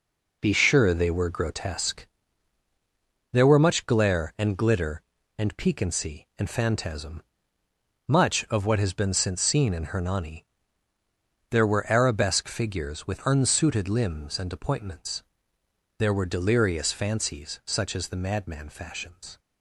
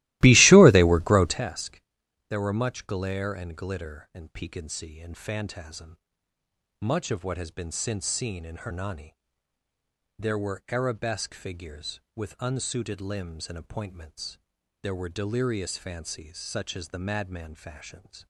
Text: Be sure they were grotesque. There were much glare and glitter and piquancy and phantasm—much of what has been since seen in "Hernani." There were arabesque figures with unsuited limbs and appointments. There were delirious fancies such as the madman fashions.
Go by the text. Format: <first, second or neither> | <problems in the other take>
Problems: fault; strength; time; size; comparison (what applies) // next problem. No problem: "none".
first | starts louder than the rest; strong; until 1.4 s; 18 dB